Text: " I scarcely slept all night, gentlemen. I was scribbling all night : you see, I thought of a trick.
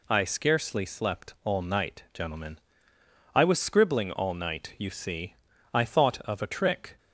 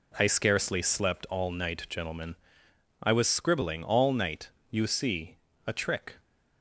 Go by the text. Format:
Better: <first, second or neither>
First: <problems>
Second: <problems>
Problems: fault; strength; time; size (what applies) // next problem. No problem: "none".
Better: first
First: none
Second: skips "I thought of"; at 5.5 s